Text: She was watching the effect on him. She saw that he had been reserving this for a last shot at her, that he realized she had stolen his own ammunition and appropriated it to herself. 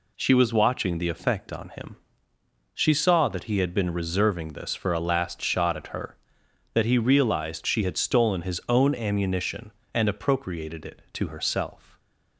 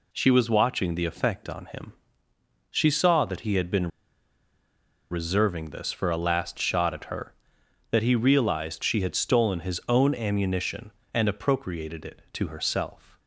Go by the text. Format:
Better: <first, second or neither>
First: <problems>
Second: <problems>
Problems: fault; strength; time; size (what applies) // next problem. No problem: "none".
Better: first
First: none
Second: pauses between "been" and "reserving"; at 3.8 s; 1.2 s long